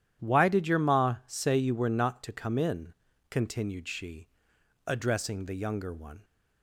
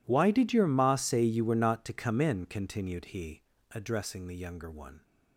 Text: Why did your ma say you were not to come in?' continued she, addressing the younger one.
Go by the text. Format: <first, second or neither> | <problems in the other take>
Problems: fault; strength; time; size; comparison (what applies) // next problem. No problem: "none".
first | says "he" for "she"; at 3.1 s